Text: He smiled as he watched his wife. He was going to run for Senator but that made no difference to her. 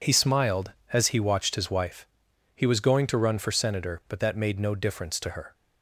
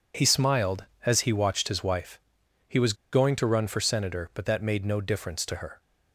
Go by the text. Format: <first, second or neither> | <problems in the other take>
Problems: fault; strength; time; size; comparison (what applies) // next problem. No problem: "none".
first | pauses between "was" and "going"; slight; at 2.9 s; 0.18 s long